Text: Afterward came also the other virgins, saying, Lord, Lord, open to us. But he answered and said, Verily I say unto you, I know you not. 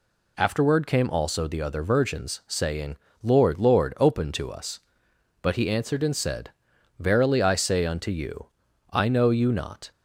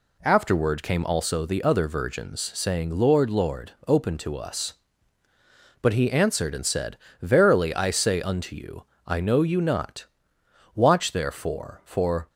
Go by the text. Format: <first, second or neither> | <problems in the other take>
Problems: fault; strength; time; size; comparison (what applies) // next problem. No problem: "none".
first | goes on to say "Watch therefore for"; from 10.7 s on; 1.5 s long